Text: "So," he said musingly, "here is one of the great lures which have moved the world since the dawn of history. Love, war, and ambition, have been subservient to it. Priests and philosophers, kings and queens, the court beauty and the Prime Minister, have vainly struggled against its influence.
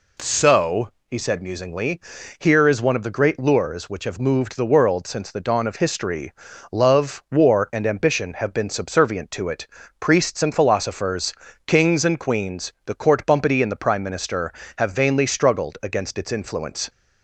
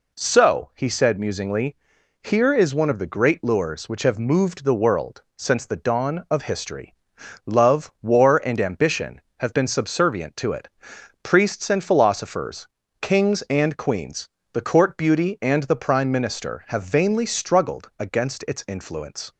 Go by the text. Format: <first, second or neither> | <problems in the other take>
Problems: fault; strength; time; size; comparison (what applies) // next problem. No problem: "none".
second | says "bumpety" for "beauty"; at 13.2 s